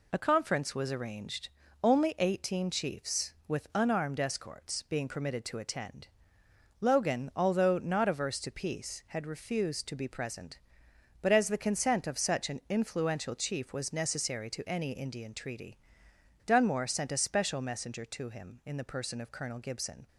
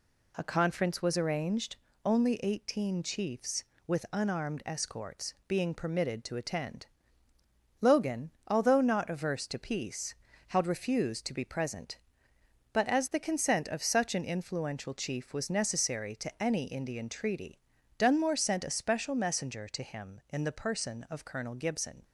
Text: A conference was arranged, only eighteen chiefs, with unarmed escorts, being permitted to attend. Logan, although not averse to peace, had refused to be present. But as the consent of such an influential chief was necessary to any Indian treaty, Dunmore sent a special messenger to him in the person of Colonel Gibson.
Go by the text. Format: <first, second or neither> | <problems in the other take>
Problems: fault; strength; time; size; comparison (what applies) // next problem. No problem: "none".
neither | none